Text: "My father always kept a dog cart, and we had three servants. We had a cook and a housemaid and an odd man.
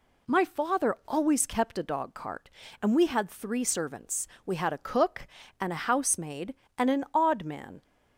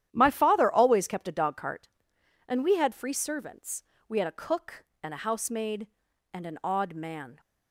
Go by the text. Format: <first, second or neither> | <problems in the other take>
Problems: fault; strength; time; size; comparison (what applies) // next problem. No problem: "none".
first | starts louder than the rest; strong; until 1.1 s; 11 dB // says "free" for "three"; at 2.9 s